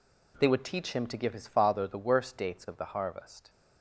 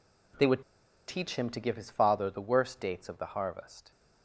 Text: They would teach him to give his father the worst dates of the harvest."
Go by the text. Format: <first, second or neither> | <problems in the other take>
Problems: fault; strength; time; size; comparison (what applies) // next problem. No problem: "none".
first | pauses between "would" and "teach"; at 0.6 s; 0.44 s long